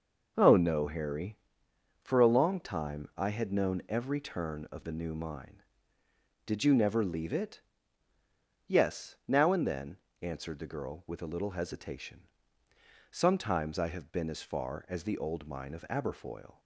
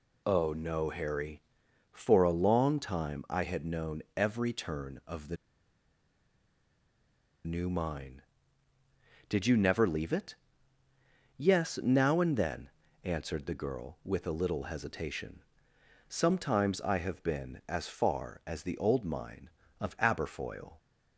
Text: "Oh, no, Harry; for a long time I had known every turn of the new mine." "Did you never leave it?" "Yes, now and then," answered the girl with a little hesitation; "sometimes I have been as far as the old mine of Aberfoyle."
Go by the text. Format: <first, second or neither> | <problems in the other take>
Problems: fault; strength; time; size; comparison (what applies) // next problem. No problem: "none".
first | pauses between "the" and "new"; strong; at 5.3 s; 2.0 s long